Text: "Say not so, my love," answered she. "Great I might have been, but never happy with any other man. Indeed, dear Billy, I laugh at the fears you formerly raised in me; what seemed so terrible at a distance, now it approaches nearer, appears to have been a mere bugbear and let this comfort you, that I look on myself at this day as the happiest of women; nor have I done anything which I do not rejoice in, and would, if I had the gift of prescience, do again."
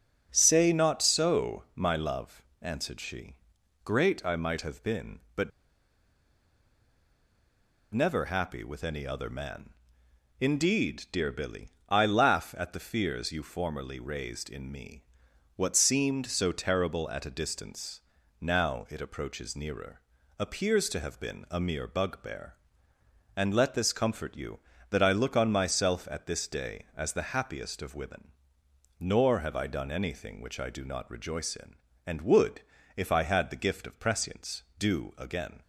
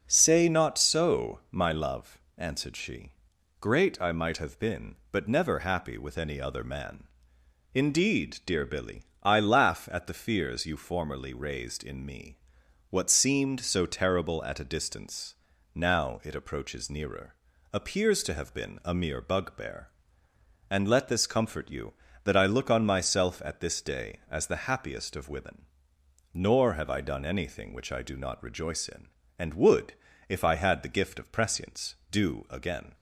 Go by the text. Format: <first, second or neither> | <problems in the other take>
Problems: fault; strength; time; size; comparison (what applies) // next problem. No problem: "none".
second | starts louder than the rest; until 1.3 s; 6.5 dB; also in the second // pauses between "but" and "never"; strong; at 5.5 s; 2.4 s long